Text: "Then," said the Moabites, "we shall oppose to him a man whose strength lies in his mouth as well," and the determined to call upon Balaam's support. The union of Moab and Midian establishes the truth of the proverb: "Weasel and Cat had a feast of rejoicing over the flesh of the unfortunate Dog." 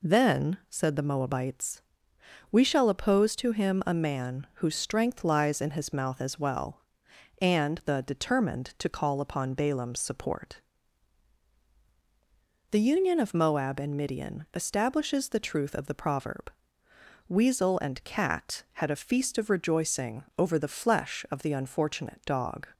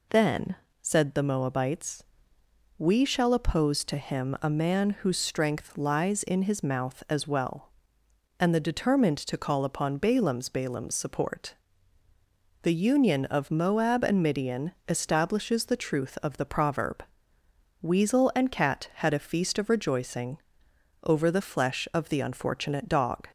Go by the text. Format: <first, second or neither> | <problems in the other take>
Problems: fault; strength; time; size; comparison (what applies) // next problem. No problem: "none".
first | says "Balaam's" twice; at 10.4 s // pauses between "rejoicing" and "over"; noticeable; at 20.3 s; 0.64 s long